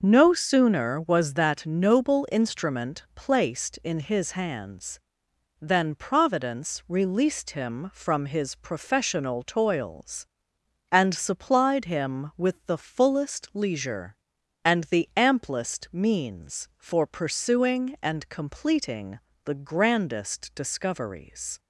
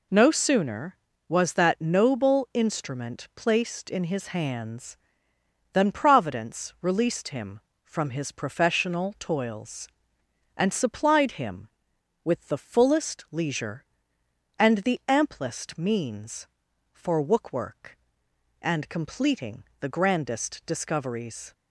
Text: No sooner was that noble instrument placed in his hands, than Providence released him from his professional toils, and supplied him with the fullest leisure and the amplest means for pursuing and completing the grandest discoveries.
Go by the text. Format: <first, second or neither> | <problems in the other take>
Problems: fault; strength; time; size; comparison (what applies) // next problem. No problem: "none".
first | says "wookwork" for "pursuing"; at 17.2 s // pauses between "completing" and "the"; slight; at 19.6 s; 0.16 s long; slight in the first